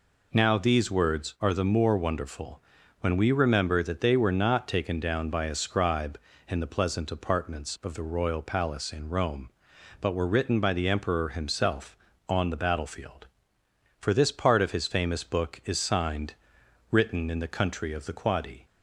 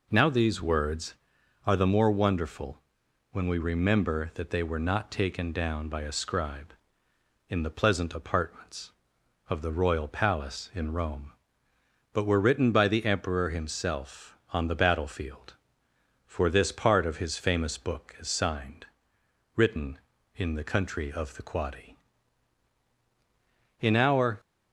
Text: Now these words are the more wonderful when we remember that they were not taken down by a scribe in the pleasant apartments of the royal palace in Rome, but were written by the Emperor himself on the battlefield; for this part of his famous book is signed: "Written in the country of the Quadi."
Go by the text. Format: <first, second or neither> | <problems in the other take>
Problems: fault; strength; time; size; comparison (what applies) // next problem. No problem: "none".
first | pauses between "wonderful" and "when"; noticeable; at 2.7 s; 0.52 s long; also in the first // goes on to say "In our"; from 23.7 s on; 0.60 s long